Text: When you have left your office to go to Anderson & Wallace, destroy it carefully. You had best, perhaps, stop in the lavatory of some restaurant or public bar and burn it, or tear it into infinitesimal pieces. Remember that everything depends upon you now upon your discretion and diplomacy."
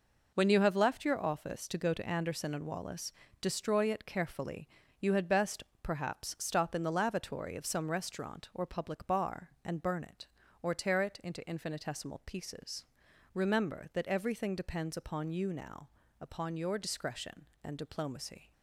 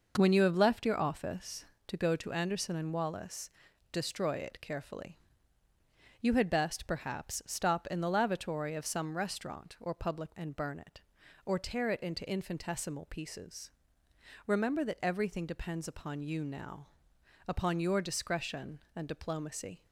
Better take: first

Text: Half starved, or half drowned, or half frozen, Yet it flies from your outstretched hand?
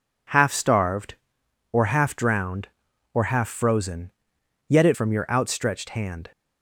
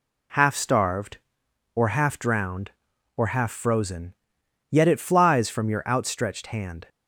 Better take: second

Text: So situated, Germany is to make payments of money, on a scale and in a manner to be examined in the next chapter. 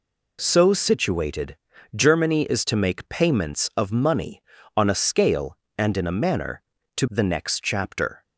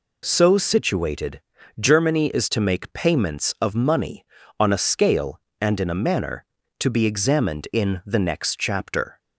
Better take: second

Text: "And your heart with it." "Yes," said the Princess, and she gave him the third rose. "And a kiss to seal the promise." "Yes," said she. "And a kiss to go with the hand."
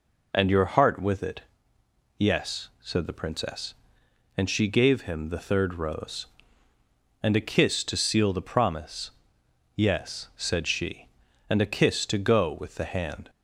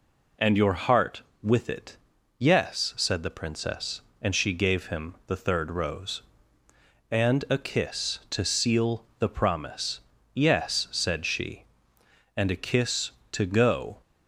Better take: first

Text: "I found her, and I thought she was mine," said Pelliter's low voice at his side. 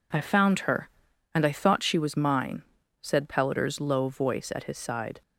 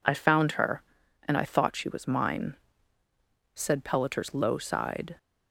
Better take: first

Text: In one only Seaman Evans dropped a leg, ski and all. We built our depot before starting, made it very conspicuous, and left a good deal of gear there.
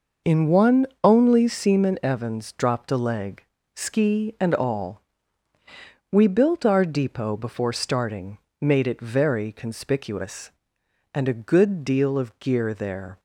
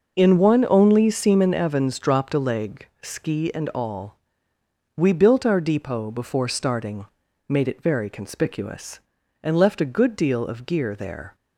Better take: second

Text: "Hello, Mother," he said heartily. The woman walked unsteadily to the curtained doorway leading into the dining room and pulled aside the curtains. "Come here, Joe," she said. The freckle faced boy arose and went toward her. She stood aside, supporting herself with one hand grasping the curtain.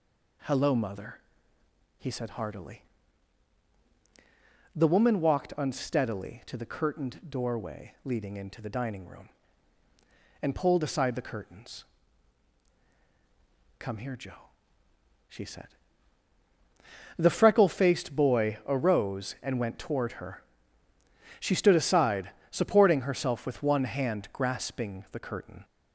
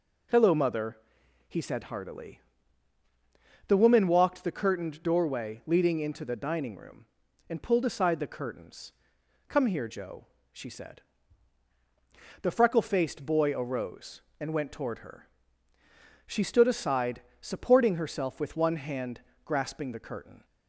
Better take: first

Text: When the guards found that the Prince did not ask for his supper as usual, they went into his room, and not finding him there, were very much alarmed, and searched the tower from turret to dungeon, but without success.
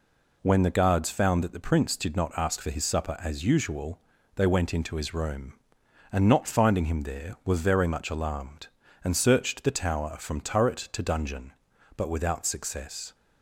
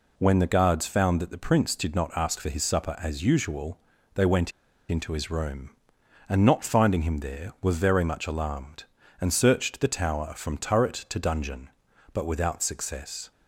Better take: first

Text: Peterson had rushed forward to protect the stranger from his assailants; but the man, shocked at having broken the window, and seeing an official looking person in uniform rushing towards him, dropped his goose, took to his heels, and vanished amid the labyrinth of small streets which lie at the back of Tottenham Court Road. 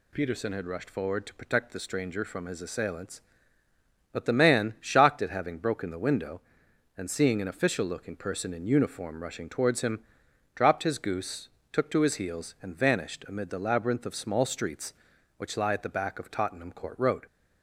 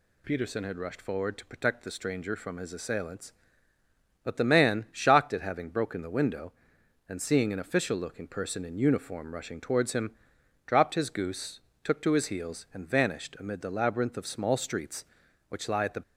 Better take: first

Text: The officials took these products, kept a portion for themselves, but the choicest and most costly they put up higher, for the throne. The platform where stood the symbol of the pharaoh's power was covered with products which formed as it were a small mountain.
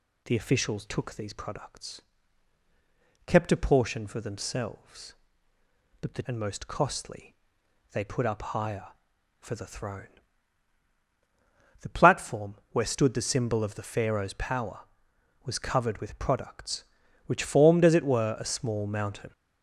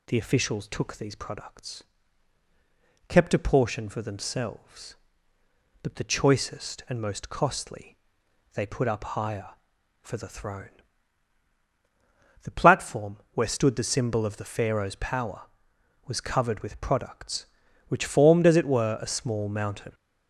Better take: second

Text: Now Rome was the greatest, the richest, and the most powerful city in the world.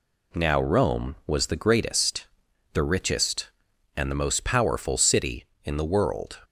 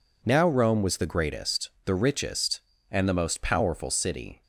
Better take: first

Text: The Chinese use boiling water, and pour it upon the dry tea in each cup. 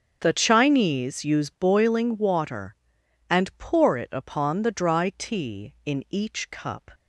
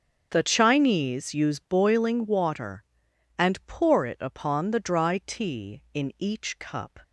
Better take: neither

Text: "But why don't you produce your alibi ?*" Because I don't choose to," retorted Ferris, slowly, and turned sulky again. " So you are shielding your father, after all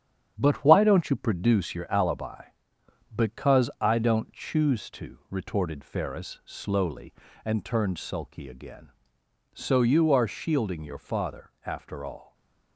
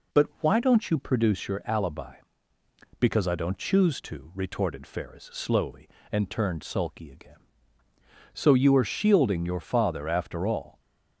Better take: second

